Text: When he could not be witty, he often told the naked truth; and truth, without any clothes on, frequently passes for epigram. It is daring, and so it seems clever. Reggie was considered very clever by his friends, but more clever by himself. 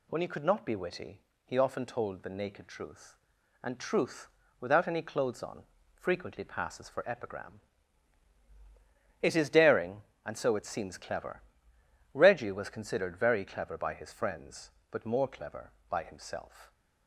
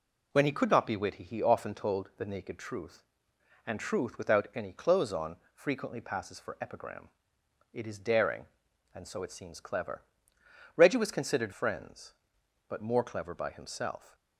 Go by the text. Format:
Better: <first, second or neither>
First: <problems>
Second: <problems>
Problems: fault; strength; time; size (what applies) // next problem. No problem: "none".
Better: first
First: none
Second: skips "very clever by his"; at 11.5 s